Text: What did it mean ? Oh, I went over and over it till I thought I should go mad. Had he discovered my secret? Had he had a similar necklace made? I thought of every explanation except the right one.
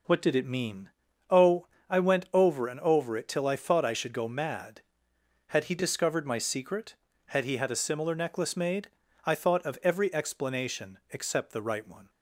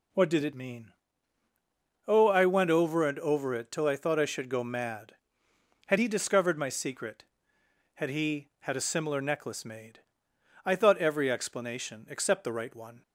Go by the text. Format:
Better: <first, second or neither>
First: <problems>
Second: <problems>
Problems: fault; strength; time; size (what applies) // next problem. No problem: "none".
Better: first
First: none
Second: skips "of"; at 10.9 s